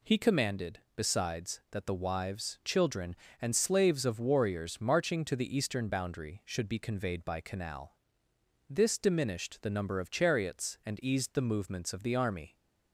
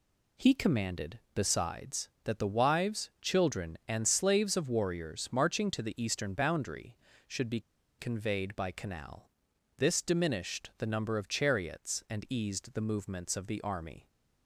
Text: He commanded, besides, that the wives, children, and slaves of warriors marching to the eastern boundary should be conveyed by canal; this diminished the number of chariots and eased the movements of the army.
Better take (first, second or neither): first